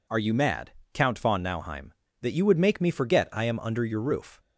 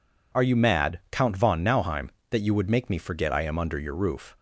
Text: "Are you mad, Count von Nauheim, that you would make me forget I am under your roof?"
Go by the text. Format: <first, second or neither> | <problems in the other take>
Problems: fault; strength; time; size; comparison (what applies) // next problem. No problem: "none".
neither | none